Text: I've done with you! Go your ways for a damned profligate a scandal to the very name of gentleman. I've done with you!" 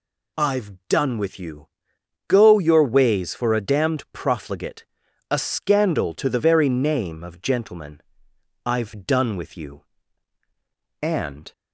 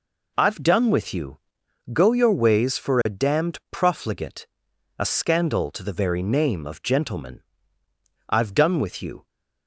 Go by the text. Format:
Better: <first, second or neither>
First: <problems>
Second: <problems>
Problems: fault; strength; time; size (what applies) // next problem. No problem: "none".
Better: second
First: pauses between "I've" and "done"; slight; at 0.7 s; 0.16 s long // pauses between "profligate" and "a"; noticeable; at 4.8 s; 0.48 s long // goes on to say "And"; from 11.0 s on; 0.50 s long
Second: pauses between "profligate" and "a"; noticeable; at 4.4 s; 0.54 s long